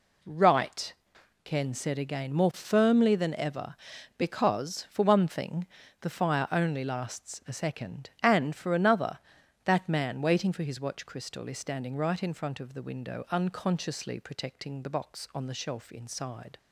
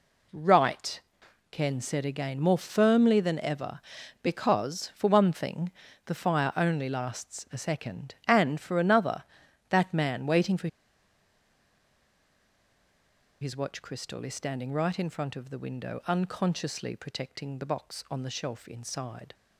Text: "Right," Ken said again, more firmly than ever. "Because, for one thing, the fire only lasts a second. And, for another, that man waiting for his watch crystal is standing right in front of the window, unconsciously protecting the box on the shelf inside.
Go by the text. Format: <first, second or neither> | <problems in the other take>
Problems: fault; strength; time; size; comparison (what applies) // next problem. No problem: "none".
first | pauses between "for" and "his"; strong; at 10.6 s; 2.7 s long